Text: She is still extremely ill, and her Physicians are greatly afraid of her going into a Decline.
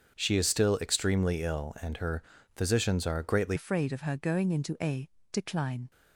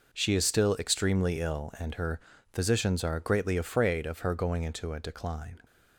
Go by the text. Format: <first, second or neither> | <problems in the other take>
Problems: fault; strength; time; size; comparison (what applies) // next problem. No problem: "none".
second | starts louder than the rest; until 1.1 s; 7 dB // pauses between "her" and "Physicians"; slight; at 2.2 s; 0.32 s long; slight in the second // changes voice at "afraid"; from 3.5 s on; 2.4 s long // pauses between "a" and "Decline"; slight; at 5.0 s; 0.26 s long